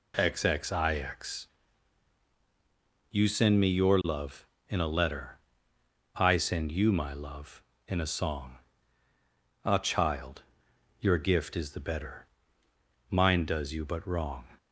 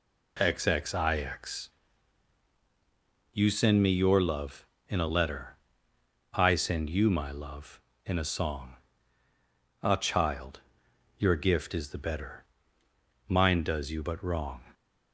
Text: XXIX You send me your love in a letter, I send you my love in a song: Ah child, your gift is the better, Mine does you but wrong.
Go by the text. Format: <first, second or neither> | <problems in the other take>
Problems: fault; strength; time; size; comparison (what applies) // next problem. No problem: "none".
neither | pauses between "XXIX" and "You"; strong; the same in both